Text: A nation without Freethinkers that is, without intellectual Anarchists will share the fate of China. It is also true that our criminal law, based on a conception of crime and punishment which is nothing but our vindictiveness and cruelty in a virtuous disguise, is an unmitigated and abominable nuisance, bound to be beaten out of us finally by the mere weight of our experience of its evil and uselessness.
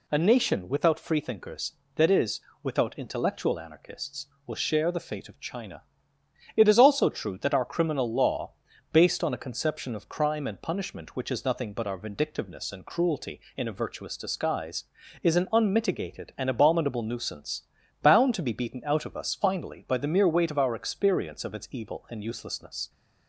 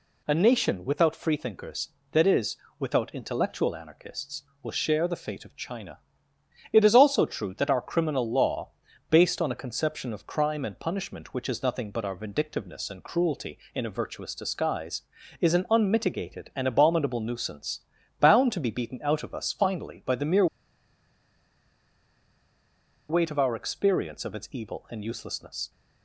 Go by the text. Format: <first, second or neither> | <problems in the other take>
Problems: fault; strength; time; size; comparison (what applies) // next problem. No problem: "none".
first | pauses between "mere" and "weight"; strong; at 20.4 s; 2.6 s long